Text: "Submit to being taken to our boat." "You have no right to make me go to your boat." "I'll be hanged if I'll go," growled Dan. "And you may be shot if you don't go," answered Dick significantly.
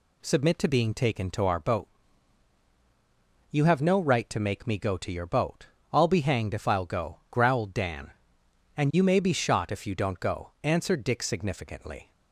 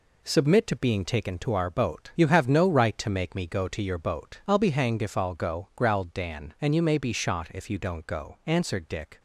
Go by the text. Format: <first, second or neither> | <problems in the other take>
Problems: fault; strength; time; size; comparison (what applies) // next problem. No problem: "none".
first | stops before "significantly"; at 9.1 s